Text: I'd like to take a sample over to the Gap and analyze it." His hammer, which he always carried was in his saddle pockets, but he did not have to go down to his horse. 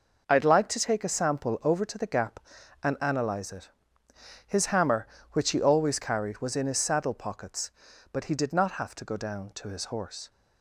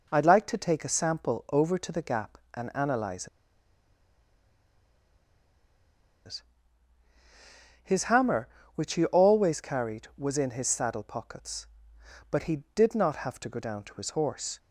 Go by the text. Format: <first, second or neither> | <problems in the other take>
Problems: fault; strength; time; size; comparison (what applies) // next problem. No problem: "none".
first | pauses between "analyze" and "it"; strong; at 3.2 s; 2.9 s long